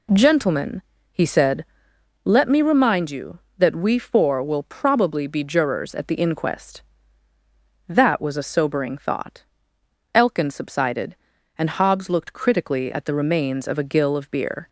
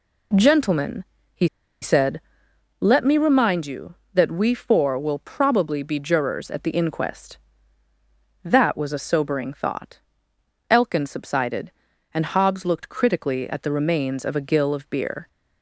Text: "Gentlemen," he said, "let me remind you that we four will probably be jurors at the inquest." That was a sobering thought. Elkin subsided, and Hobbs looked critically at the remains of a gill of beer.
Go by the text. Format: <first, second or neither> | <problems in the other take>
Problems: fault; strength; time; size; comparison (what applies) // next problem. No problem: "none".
first | pauses between "he" and "said"; slight; at 1.4 s; 0.36 s long